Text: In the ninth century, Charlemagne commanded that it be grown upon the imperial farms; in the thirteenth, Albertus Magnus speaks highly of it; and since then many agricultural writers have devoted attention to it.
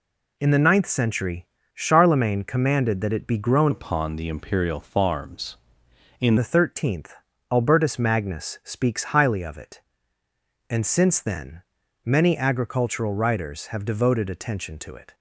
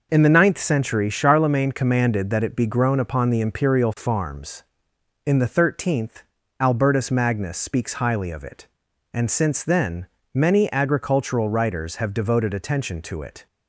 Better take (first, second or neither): second